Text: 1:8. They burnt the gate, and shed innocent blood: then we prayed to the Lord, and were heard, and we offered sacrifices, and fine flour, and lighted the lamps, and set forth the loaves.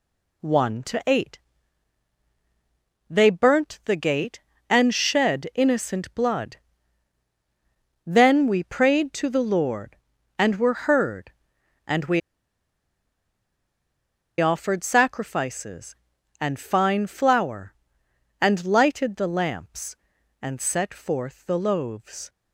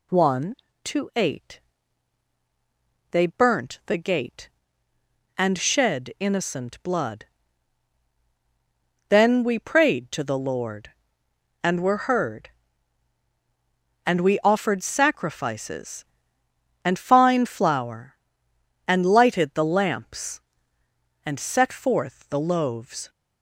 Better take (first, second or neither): second